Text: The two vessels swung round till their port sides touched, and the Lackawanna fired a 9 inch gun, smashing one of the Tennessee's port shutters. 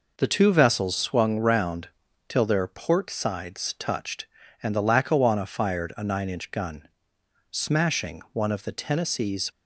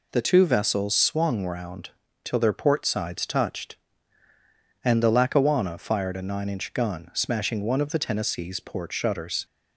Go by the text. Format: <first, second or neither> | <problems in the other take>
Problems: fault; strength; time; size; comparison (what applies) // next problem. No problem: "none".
second | pauses between "round" and "till"; at 1.8 s; 0.40 s long; slight in the second // stops before "port shutters"; at 9.4 s